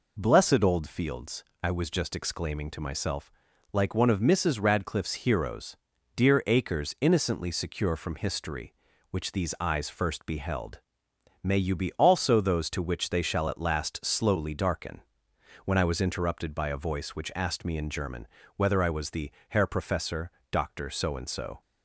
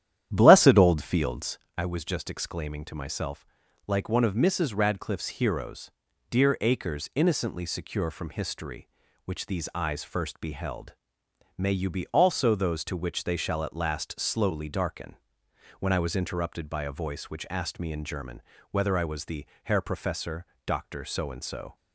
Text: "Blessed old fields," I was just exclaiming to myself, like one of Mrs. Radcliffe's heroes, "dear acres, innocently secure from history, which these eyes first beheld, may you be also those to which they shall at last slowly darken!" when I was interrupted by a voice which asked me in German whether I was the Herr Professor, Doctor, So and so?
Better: first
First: pauses between "German" and "whether"; slight; at 18.2 s; 0.28 s long // pauses between "the" and "Herr"; slight; at 19.2 s; 0.20 s long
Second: starts louder than the rest; strong; until 1.7 s; 10.5 dB // pauses between "German" and "whether"; slight; at 18.4 s; 0.28 s long // pauses between "the" and "Herr"; slight; at 19.4 s; 0.20 s long

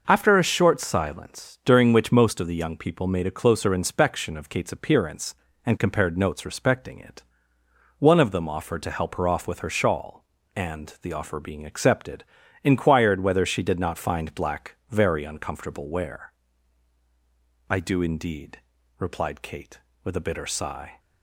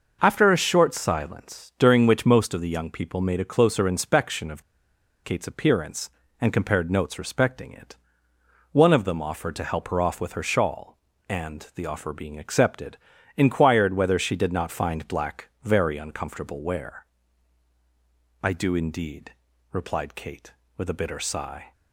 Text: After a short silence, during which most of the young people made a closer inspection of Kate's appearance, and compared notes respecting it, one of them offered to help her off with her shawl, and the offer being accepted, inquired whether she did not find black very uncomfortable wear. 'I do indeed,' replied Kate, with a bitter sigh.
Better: first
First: none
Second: pauses between "of" and "Kate's"; noticeable; at 4.6 s; 0.61 s long

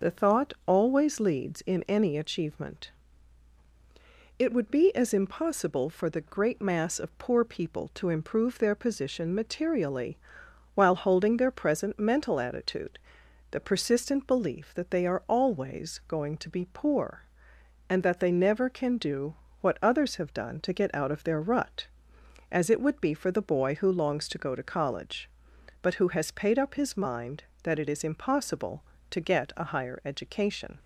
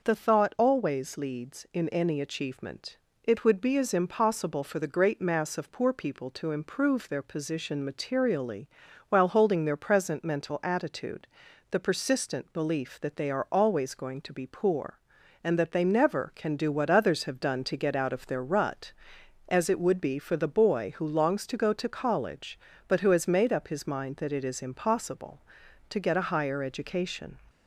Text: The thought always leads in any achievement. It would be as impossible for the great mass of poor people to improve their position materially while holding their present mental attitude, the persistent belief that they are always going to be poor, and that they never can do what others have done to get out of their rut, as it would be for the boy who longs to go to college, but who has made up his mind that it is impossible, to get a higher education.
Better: second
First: pauses between "materially" and "while"; noticeable; at 10.1 s; 0.56 s long // pauses between "do" and "what"; slight; at 19.3 s; 0.26 s long // says "paid" for "made"; at 26.3 s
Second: pauses between "materially" and "while"; at 8.6 s; 0.44 s long

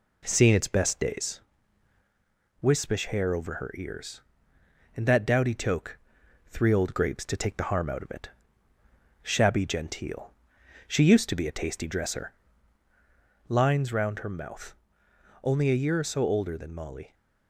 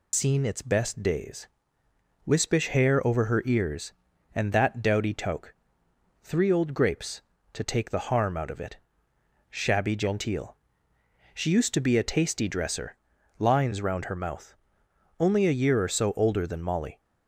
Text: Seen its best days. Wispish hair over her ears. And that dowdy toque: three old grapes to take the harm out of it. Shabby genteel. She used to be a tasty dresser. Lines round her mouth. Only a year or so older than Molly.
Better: first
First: none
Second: loses the start of "Seen"; at 0.1 s; 100 ms

